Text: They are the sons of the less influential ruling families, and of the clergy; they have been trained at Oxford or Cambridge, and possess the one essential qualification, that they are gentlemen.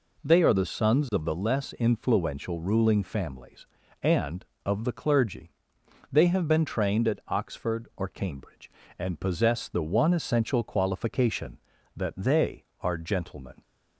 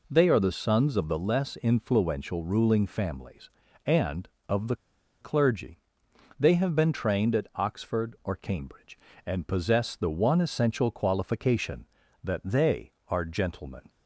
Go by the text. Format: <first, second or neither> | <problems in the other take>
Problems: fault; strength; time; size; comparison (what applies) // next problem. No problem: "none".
first | pauses between "the" and "clergy"; at 4.7 s; 0.45 s long